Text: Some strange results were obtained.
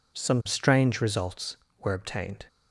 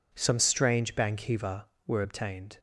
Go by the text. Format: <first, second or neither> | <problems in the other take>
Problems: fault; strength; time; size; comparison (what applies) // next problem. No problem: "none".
first | says "bankiva" for "results"; at 0.9 s